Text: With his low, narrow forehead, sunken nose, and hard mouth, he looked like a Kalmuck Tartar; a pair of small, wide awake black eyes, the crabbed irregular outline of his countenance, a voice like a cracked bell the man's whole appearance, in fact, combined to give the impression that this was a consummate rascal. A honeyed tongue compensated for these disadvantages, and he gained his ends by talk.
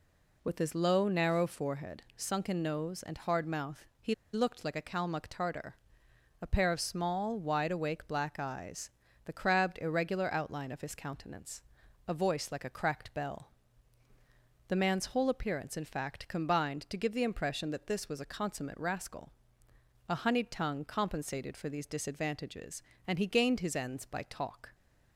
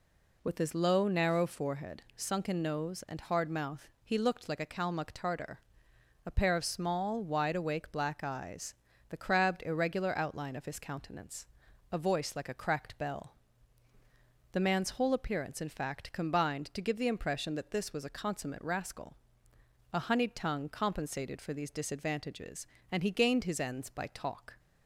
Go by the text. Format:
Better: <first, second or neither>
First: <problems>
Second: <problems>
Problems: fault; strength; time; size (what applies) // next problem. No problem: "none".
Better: second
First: pauses between "he" and "looked"; slight; at 4.1 s; 0.19 s long // pauses between "bell" and "the"; at 13.5 s; 1.1 s long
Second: pauses between "bell" and "the"; at 13.3 s; 1.1 s long